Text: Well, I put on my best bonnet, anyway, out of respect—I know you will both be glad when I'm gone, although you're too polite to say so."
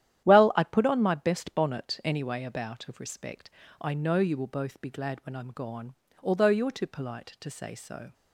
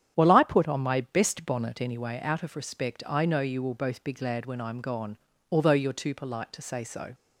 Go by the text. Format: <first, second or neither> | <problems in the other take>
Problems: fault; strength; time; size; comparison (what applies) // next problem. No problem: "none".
second | starts louder than the rest; strong; until 1.2 s; 11 dB; strong in the second // says "about" for "out"; at 2.4 s